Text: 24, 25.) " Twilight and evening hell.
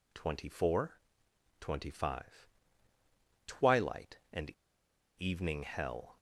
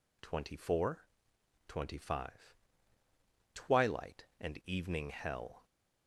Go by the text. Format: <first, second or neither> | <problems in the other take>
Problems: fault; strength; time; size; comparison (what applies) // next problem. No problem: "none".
second | pauses between "and" and "evening"; noticeable; at 4.5 s; 0.68 s long